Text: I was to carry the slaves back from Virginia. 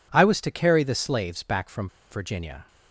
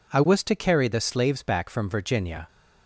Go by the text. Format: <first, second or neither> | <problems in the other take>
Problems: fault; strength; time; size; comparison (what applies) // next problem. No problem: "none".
second | pauses between "from" and "Virginia"; slight; at 1.8 s; 0.23 s long